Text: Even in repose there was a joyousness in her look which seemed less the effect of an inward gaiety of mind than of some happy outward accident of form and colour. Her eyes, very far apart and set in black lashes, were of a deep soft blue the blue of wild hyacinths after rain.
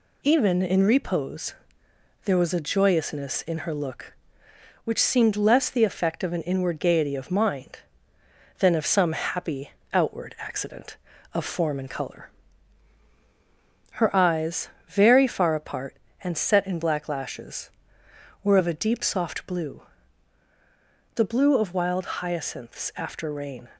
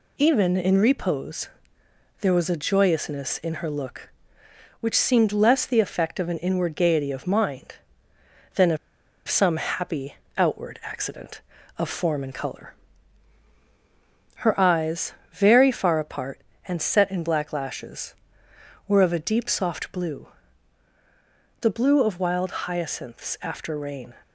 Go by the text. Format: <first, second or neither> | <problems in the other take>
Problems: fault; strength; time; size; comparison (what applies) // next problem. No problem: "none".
first | pauses between "repose" and "there"; noticeable; at 1.4 s; 0.72 s long; noticeable in the first // pauses between "of" and "some"; noticeable; at 8.7 s; 0.50 s long // pauses between "happy" and "outward"; slight; at 10.1 s; 0.22 s long; slight in the first // pauses between "blue" and "the"; strong; at 20.2 s; 1.3 s long; strong in the first